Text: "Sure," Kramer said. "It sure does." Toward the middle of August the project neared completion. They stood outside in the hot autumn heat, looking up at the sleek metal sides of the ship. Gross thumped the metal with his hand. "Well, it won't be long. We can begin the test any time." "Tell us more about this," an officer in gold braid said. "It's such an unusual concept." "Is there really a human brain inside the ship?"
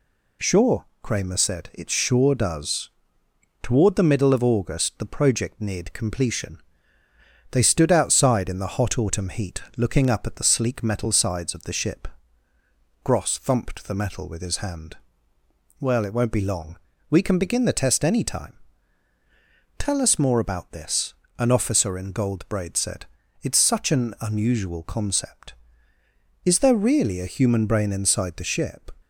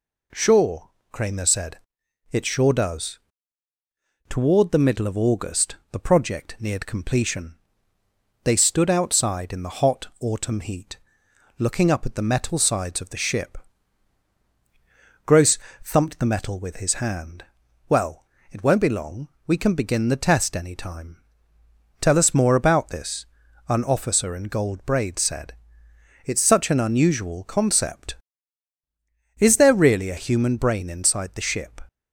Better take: first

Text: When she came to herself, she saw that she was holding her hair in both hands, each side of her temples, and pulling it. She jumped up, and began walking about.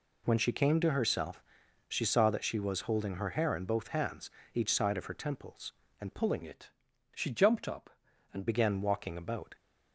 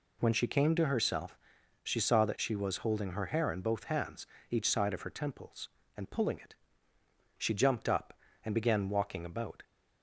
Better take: second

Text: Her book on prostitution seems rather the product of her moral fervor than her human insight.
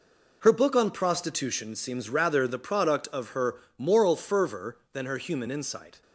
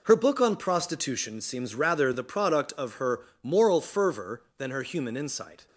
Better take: neither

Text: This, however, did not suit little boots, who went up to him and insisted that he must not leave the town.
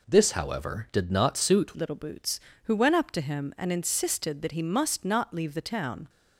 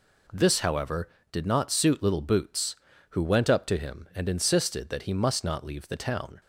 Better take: second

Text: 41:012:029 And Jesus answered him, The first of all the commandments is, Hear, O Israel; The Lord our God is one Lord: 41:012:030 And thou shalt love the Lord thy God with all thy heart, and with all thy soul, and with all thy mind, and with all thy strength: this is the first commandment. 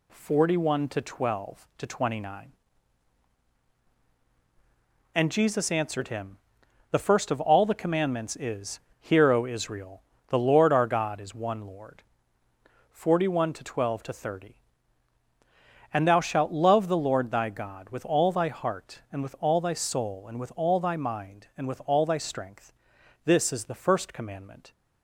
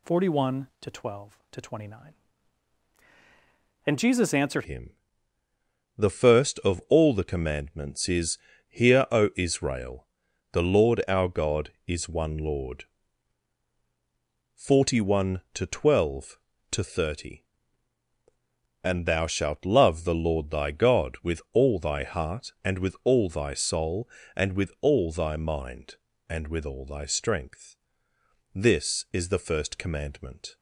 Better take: first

